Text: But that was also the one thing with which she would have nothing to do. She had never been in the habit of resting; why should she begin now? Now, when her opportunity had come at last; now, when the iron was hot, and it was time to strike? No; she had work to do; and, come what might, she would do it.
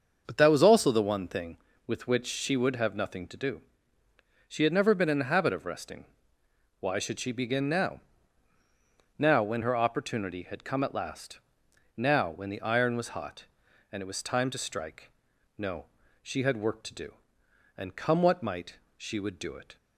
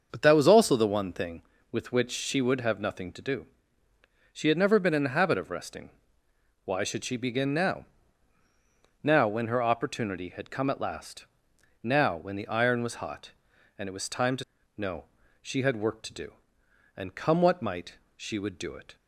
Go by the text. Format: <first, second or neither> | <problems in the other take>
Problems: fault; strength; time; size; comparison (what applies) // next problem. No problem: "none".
first | starts louder than the rest; until 1.1 s; 6.5 dB; also in the first // skips "strike"; at 14.6 s